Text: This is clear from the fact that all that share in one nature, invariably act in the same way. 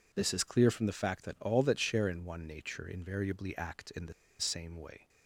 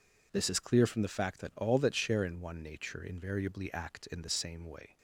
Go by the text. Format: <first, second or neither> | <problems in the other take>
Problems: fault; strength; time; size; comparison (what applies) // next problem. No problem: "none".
second | pauses between "the" and "same"; slight; at 4.1 s; 0.27 s long